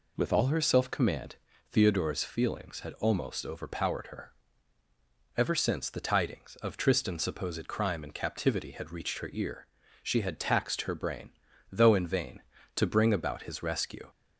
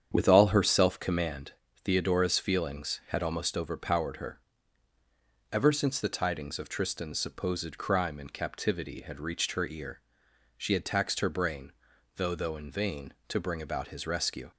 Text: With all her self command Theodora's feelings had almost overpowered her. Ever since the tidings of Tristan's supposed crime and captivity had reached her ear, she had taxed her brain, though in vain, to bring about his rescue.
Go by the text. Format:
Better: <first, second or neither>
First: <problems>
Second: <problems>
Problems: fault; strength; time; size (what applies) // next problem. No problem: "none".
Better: first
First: pauses between "command" and "Theodora's"; slight; at 1.3 s; 0.36 s long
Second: starts louder than the rest; strong; until 1.1 s; 8 dB // pauses between "command" and "Theodora's"; slight; at 1.5 s; 0.32 s long // says "though" twice; at 12.3 s